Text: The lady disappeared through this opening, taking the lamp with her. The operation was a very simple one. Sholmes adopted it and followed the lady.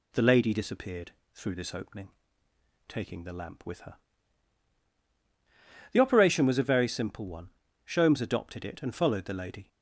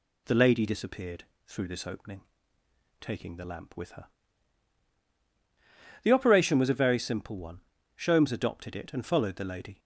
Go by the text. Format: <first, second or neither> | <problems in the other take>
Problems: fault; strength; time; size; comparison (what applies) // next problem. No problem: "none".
neither | pauses between "disappeared" and "through"; slight; the same in both